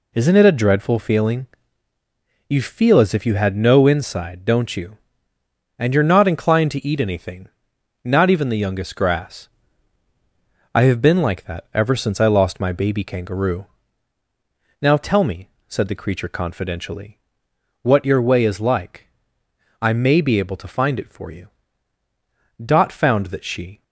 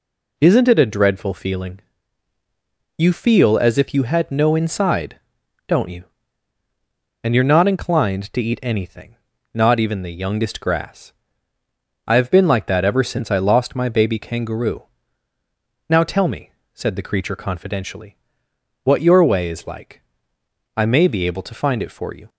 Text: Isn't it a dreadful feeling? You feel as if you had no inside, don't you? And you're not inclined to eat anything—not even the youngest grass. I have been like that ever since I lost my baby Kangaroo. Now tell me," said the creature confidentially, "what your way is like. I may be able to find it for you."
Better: second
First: goes on to say "Dot found that she"; noticeable; from 22.6 s on; 1.2 s long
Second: none

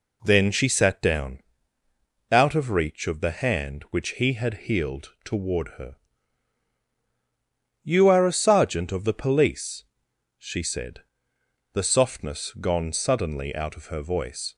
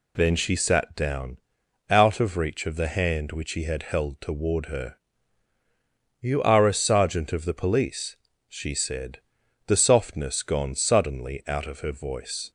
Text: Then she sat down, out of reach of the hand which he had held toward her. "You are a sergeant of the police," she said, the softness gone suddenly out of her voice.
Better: second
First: says "healed" for "held"; at 4.6 s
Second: none

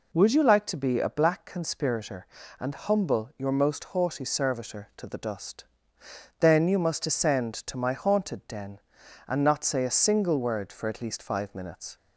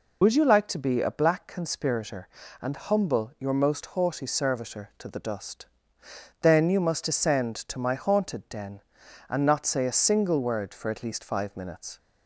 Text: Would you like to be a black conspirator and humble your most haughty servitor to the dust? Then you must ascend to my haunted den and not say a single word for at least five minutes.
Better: first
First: none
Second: loses the start of "Would"; at 0.2 s; 60 ms

